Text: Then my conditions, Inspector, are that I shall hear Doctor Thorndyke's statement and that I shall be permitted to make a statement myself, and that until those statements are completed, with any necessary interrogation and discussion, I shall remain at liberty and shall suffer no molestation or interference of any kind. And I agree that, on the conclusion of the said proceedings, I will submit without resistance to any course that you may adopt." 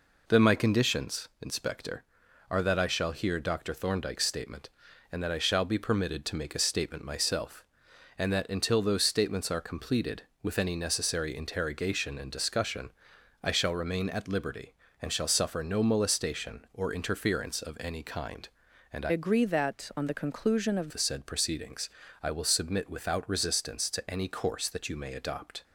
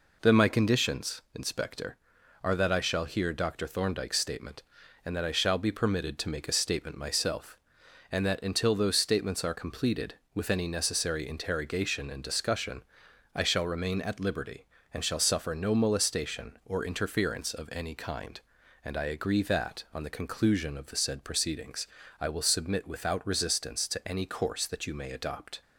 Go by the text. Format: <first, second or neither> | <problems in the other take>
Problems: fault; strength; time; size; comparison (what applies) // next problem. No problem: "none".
second | changes voice from "agree" to "of"; from 19.0 to 20.8 s; 1.8 s long